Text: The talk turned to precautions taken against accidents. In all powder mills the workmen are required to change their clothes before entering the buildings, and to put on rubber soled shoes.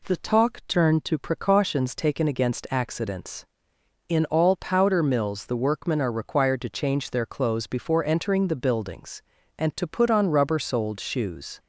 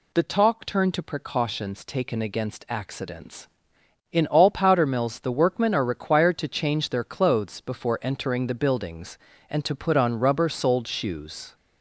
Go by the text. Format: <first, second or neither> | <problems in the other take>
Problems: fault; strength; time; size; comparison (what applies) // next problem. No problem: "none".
first | gets louder; throughout; 3.5 dB